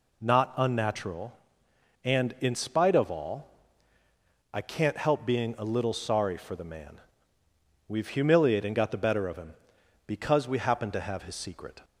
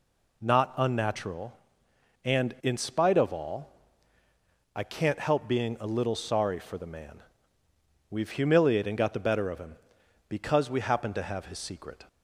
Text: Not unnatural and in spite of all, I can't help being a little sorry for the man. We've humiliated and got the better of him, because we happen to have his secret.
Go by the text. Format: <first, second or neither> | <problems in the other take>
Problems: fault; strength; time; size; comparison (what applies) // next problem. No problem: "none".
neither | none